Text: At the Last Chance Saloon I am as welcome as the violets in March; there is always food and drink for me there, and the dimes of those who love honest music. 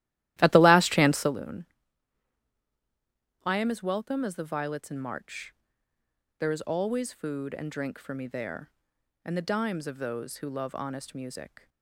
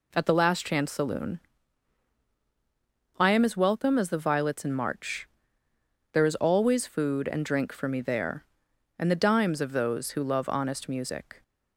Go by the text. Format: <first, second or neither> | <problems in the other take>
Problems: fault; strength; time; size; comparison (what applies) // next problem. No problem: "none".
second | starts louder than the rest; strong; until 1.3 s; 14.5 dB // pauses between "Saloon" and "I"; strong; at 1.6 s; 1.7 s long; strong in the second